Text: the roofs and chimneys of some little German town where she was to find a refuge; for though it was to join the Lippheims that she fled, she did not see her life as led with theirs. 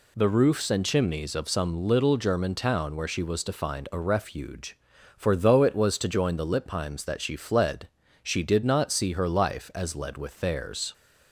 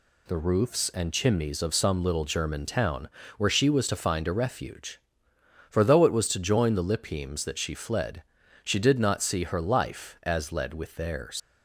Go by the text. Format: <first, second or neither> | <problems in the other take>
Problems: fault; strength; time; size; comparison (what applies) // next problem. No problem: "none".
first | pauses between "town" and "where"; slight; at 3.0 s; 0.30 s long // leaves "theirs" unfinished; at 11.3 s; 170 ms